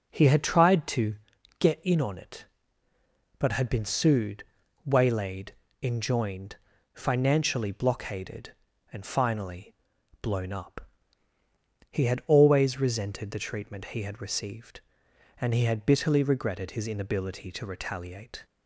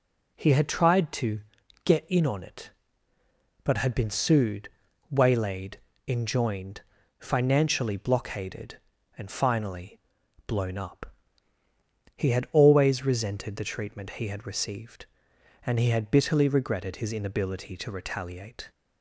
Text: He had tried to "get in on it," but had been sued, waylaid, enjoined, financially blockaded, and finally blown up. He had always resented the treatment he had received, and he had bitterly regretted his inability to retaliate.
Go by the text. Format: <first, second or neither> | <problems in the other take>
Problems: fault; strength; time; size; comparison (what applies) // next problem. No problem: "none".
second | starts louder than the rest; noticeable; until 1.2 s; 5 dB // pauses between "to" and "get"; at 1.1 s; 0.44 s long; also in the second // pauses between "finally" and "blown"; noticeable; at 9.7 s; 0.48 s long; noticeable in the second